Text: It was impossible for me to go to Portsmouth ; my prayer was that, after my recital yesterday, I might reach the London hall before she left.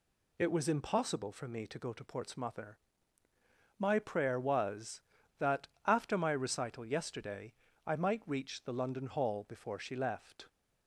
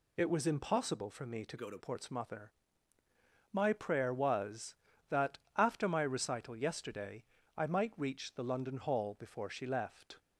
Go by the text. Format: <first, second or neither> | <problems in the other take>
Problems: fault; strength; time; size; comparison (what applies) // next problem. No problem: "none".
first | changes voice from "go" to "to"; from 1.5 to 1.7 s; 0.2 s long